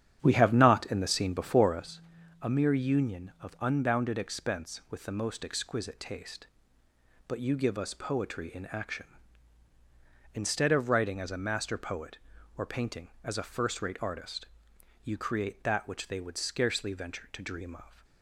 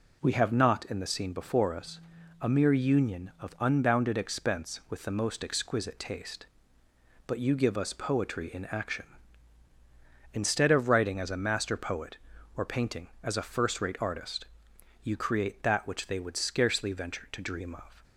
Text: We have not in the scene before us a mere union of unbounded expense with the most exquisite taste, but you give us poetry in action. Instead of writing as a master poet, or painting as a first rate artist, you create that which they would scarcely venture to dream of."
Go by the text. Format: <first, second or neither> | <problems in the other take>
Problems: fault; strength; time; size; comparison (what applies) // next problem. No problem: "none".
second | starts louder than the rest; strong; until 2.0 s; 9 dB // pauses between "us" and "a"; at 2.0 s; 0.40 s long; also in the second